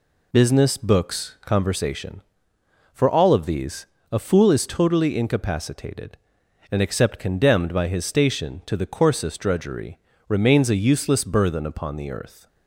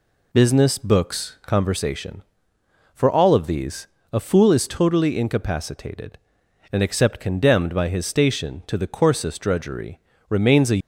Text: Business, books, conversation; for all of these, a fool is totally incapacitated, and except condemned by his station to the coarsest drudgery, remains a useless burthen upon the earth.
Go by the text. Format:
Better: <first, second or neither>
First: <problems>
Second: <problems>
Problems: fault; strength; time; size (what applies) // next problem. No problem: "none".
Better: first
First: none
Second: stops before "useless burthen upon the earth"; at 10.7 s